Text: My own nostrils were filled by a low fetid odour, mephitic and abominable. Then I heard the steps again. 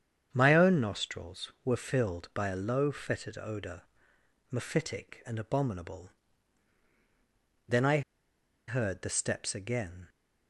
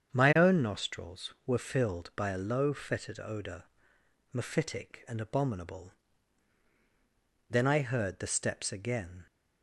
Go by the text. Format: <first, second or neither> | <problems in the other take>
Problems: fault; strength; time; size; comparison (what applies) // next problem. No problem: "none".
second | starts louder than the rest; strong; until 1.3 s; 8 dB; strong in the second // pauses between "I" and "heard"; noticeable; at 8.0 s; 0.67 s long